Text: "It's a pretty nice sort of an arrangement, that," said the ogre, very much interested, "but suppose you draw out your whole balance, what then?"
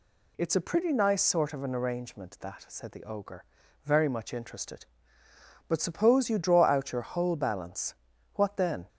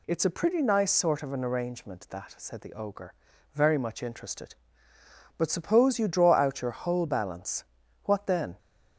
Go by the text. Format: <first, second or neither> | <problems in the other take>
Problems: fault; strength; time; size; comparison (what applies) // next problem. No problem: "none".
neither | none